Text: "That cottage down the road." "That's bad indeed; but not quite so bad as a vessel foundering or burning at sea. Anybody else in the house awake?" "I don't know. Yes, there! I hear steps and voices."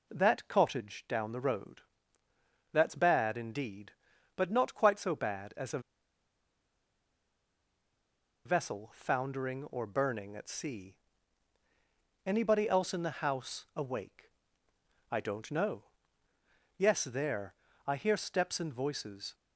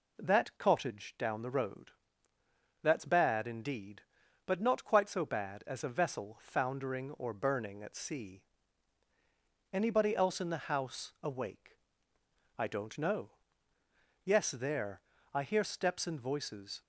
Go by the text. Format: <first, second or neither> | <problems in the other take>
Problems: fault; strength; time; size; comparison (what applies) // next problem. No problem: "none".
second | pauses between "a" and "vessel"; strong; at 5.7 s; 2.6 s long